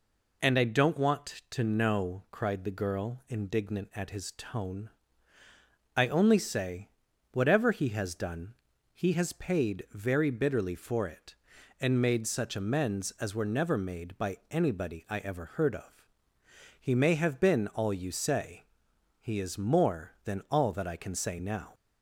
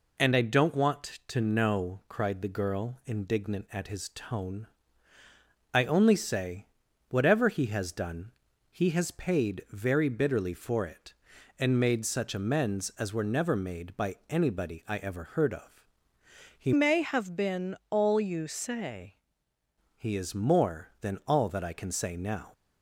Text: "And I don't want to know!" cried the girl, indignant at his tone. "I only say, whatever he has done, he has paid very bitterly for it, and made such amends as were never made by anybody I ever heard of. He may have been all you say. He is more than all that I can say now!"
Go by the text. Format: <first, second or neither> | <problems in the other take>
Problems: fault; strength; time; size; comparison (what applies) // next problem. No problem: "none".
first | changes voice from "may" to "say"; from 16.7 to 19.1 s; 2.4 s long